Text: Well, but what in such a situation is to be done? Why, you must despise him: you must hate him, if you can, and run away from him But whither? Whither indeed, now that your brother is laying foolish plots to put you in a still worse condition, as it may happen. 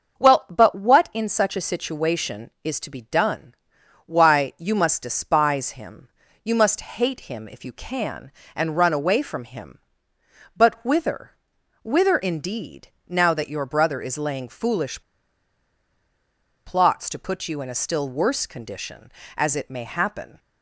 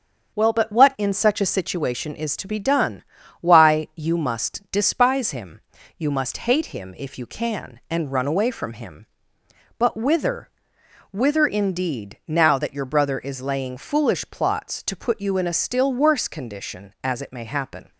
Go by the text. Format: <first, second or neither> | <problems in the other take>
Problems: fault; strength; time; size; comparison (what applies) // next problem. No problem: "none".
second | starts louder than the rest; until 1.2 s; 6.5 dB; strong in the second // pauses between "foolish" and "plots"; strong; at 15.0 s; 1.6 s long